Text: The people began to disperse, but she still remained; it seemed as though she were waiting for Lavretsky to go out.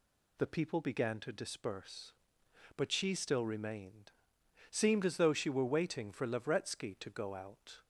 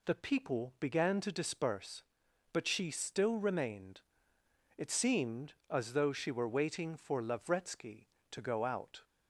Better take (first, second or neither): second